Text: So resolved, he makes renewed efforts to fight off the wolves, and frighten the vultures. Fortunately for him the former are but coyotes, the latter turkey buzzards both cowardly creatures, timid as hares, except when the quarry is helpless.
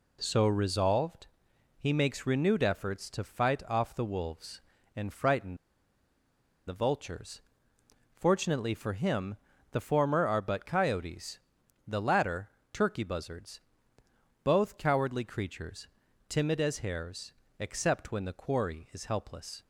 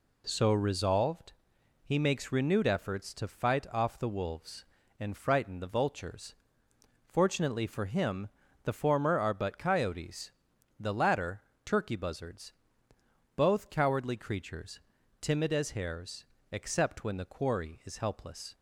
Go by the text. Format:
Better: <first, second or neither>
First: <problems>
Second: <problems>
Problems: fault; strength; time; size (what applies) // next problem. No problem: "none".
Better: second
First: pauses between "frighten" and "the"; at 5.5 s; 1.1 s long // pauses between "him" and "the"; slight; at 9.3 s; 0.34 s long // pauses between "latter" and "turkey"; slight; at 12.4 s; 0.22 s long // pauses between "buzzards" and "both"; noticeable; at 13.5 s; 0.82 s long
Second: pauses between "him" and "the"; slight; at 8.2 s; 0.34 s long // pauses between "latter" and "turkey"; slight; at 11.4 s; 0.22 s long // pauses between "buzzards" and "both"; noticeable; at 12.5 s; 0.82 s long